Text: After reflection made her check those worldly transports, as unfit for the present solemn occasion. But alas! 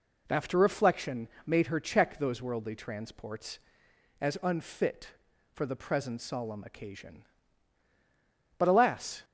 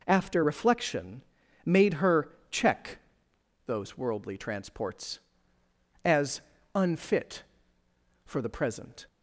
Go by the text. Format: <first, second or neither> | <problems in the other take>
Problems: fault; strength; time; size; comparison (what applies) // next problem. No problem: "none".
first | pauses between "reflection" and "made"; at 1.2 s; 0.42 s long; slight in the first // pauses between "her" and "check"; slight; at 2.2 s; 0.22 s long // pauses between "check" and "those"; noticeable; at 2.9 s; 0.68 s long // pauses between "as" and "unfit"; noticeable; at 6.4 s; 0.54 s long // stops before "solemn occasion But alas"; at 9.0 s